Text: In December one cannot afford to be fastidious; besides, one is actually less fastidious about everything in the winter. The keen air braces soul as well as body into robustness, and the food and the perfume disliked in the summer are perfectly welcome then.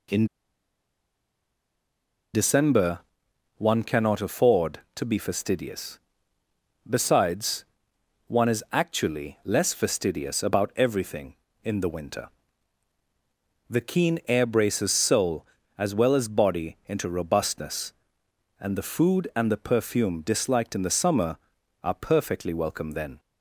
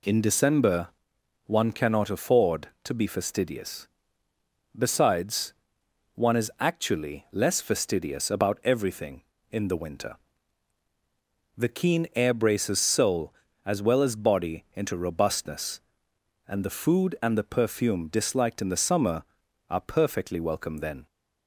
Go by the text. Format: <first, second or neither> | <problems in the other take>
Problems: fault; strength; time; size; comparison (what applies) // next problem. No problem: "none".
second | pauses between "In" and "December"; strong; at 0.2 s; 2.0 s long // pauses between "December" and "one"; noticeable; at 2.9 s; 0.58 s long; noticeable in the second